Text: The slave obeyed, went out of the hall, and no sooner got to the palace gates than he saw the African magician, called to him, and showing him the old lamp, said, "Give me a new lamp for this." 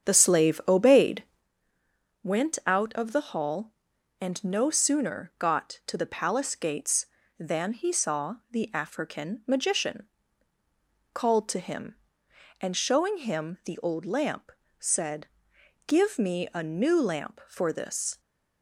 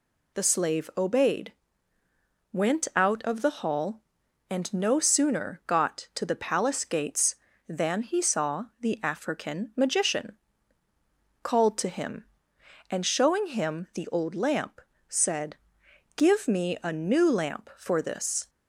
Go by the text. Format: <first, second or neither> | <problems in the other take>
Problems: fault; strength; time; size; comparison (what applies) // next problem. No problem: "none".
second | starts louder than the rest; strong; until 1.5 s; 8 dB